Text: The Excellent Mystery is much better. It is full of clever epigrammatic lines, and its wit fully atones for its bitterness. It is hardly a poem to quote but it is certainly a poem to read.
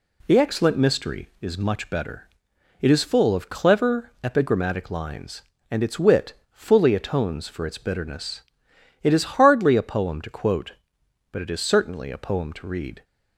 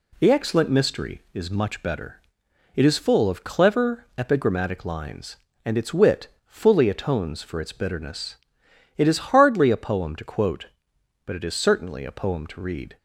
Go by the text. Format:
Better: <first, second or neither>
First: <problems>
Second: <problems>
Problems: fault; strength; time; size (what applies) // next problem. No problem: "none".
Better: neither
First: pauses between "wit" and "fully"; slight; at 6.3 s; 0.18 s long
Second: pauses between "wit" and "fully"; slight; at 6.2 s; 0.18 s long